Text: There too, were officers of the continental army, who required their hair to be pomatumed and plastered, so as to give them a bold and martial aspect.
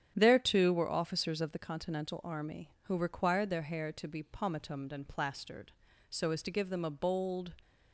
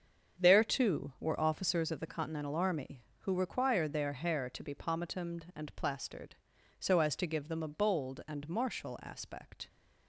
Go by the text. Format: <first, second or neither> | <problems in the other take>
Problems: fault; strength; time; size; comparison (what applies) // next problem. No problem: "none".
second | starts louder than the rest; strong; until 1.1 s; 9 dB; also in the second // stops before "and martial aspect"; at 7.6 s